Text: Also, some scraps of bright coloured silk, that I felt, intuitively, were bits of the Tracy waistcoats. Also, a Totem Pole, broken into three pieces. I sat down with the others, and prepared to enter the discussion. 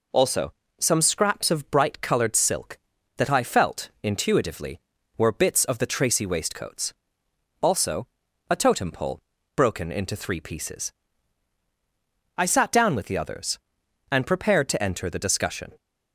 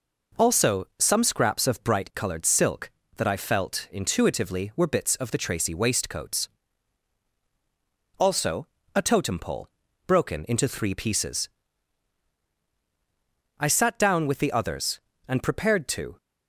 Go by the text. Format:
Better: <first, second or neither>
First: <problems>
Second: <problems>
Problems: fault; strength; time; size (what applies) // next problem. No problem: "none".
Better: first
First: none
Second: stops before "enter the discussion"; at 16.1 s